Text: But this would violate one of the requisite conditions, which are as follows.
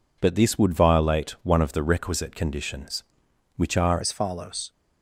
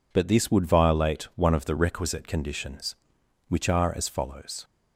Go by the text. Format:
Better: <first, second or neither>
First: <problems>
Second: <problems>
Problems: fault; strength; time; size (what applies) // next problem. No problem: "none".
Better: second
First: changes voice at "as"; from 4.0 s on; 0.7 s long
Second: none